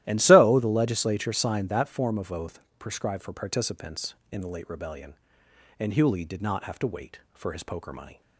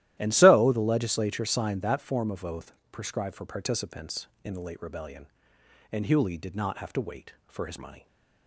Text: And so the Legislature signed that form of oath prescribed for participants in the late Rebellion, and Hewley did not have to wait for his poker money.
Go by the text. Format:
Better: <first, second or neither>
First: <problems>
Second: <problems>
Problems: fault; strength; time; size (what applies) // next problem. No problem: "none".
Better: first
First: starts louder than the rest; strong; until 1.0 s; 14 dB // pauses between "oath" and "prescribed"; slight; at 2.5 s; 0.18 s long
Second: starts louder than the rest; strong; until 1.1 s; 14 dB // pauses between "oath" and "prescribed"; slight; at 2.7 s; 0.18 s long // skips "poker"; at 7.7 s